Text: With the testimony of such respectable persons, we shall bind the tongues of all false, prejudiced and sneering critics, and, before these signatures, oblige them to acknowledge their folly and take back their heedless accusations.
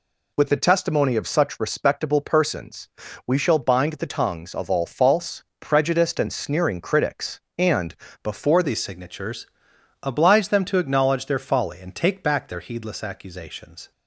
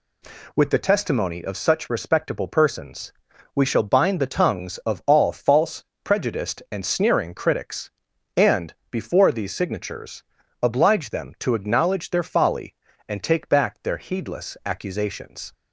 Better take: second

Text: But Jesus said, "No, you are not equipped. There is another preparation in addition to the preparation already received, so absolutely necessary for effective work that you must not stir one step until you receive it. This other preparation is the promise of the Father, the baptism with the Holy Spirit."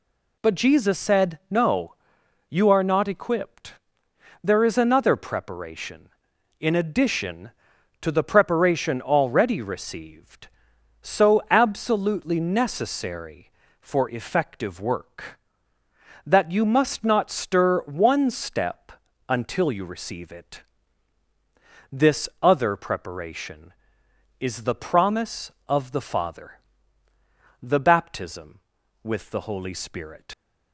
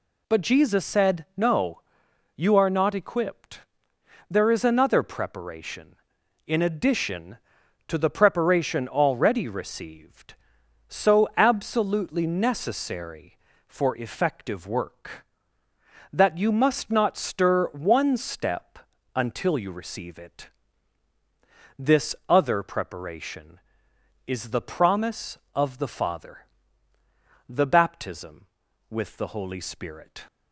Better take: second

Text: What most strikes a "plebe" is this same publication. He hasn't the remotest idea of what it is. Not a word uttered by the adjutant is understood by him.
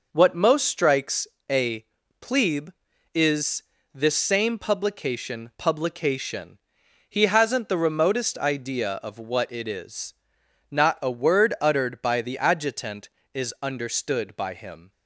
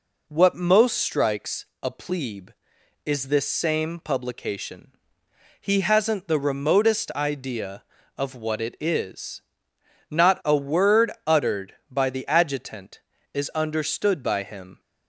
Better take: second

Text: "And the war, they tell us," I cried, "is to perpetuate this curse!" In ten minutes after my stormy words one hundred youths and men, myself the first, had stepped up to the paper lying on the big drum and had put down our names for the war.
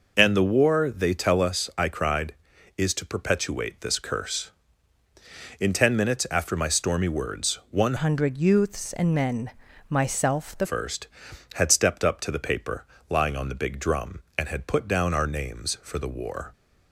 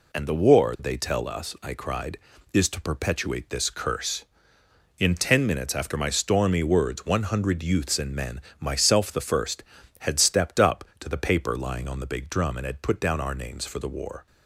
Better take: second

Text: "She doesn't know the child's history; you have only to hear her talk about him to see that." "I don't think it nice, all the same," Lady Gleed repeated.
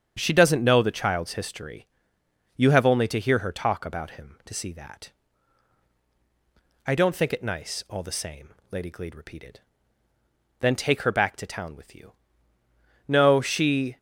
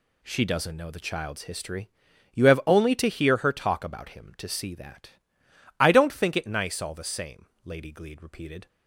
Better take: second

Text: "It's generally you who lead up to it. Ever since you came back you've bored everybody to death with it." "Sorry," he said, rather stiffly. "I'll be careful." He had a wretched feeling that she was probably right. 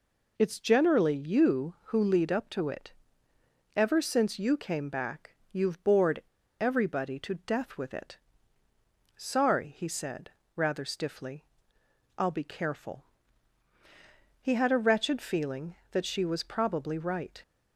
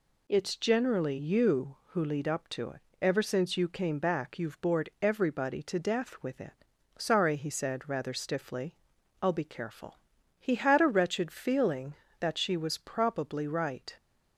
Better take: second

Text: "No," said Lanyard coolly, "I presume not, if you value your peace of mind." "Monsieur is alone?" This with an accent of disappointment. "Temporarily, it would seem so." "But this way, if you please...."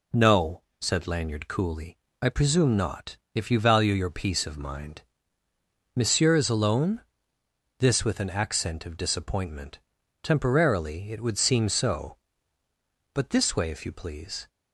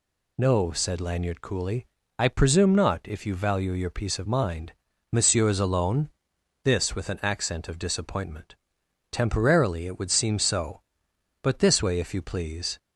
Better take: neither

